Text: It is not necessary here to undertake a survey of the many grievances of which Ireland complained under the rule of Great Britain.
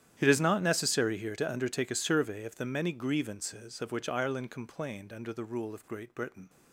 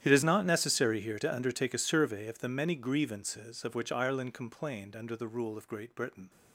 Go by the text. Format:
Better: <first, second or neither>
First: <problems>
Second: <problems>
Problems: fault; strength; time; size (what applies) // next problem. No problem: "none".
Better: neither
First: starts louder than the rest; strong; until 1.1 s; 11 dB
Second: starts louder than the rest; strong; until 1.0 s; 11 dB